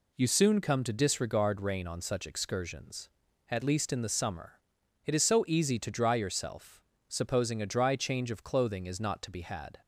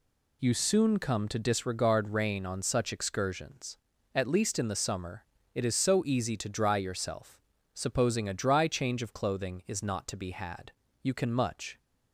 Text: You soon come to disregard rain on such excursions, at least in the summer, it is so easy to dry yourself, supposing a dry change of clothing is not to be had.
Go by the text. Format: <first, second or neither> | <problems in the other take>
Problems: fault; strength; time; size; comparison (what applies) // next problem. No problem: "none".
first | goes on to say "You can much"; noticeable; from 11.0 s on; 0.76 s long